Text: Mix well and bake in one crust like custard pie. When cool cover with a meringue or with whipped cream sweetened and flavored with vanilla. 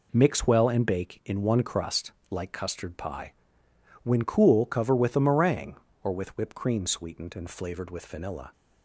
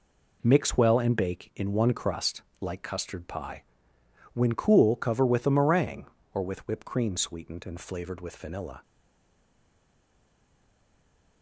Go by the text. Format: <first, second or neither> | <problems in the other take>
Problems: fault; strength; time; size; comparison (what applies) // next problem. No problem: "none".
first | pauses between "crust" and "like"; slight; at 2.3 s; 0.22 s long; slight in the first // stays silent after the last word; strong; from 8.8 s on; 2.6 s long